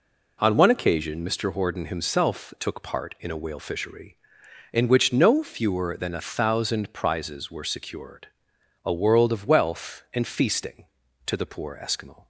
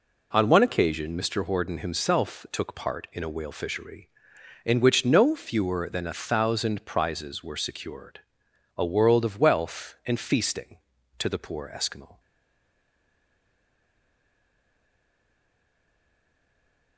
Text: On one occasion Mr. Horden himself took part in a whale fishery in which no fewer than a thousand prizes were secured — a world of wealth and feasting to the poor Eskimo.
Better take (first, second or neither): first